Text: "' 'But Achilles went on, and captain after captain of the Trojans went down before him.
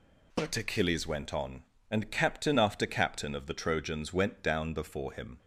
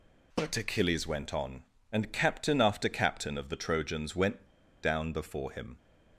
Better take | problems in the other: first | pauses between "went" and "down"; at 4.4 s; 0.38 s long

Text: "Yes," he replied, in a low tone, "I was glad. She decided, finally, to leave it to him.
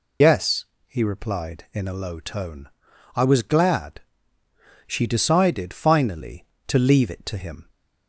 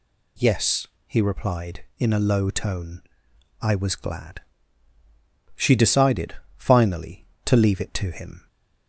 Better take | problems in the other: second | loses the start of "Yes"; at 0.2 s; 55 ms

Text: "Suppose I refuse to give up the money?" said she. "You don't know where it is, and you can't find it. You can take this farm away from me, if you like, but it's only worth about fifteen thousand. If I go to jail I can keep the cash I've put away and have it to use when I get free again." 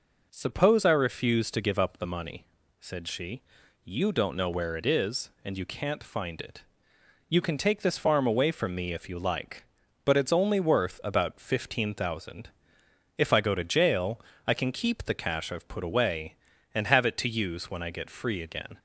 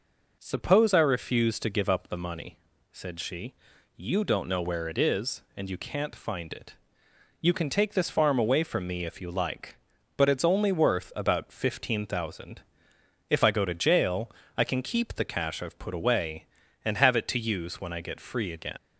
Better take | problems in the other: first | pauses between "jail" and "I"; slight; at 14.3 s; 0.28 s long; slight in the first // leaves "again" unfinished; at 18.7 s; 105 ms

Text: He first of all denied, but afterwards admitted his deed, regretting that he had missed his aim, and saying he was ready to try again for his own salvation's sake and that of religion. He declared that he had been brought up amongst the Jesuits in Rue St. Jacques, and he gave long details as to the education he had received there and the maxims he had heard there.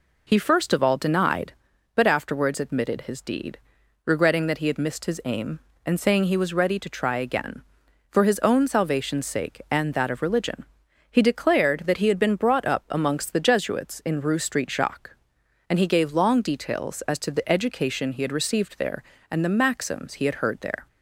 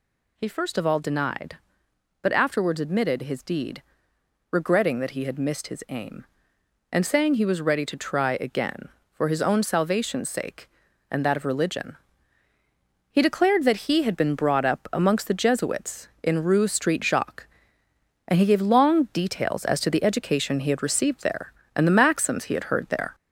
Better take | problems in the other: first | gets louder; throughout; 3.5 dB

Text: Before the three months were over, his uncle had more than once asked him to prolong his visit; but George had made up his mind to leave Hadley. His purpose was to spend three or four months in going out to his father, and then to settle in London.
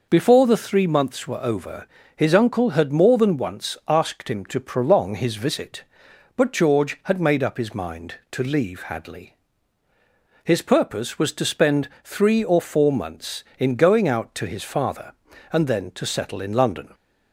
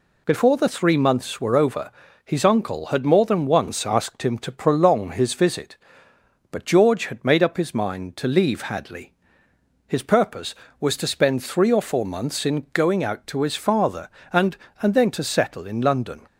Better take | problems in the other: first | says "and" twice; at 14.7 s

